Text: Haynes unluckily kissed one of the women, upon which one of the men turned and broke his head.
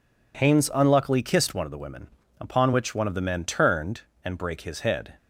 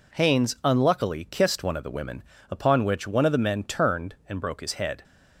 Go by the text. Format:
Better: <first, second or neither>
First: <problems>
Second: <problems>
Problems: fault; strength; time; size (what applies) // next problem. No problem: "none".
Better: second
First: says "brake" for "broke"; at 4.3 s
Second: none